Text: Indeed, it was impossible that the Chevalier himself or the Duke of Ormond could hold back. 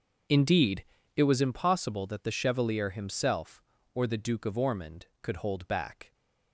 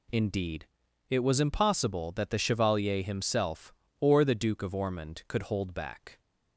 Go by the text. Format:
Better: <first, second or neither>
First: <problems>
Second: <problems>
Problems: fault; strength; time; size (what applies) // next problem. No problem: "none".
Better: second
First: starts louder than the rest; noticeable; until 1.4 s; 6 dB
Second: none